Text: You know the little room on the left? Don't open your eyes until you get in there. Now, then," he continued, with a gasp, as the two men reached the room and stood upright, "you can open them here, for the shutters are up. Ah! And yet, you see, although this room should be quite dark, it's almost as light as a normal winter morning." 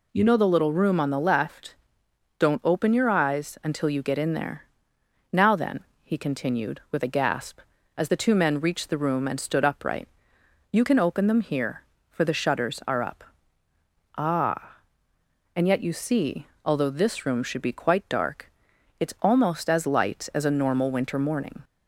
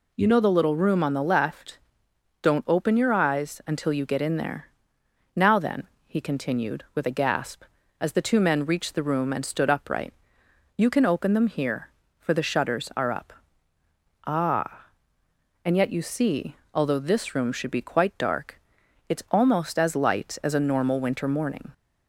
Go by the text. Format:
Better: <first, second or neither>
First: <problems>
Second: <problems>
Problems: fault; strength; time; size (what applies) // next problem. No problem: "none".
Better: neither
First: none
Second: none